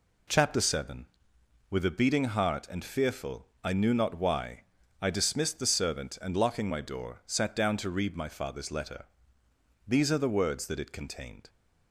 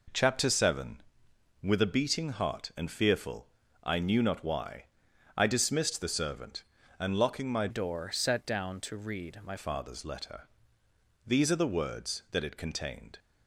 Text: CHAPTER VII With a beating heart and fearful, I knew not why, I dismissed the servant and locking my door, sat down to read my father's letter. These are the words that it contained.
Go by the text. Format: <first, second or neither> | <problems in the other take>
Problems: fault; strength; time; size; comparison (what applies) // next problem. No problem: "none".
first | changes voice from "door" to "my"; from 7.6 to 9.5 s; 1.9 s long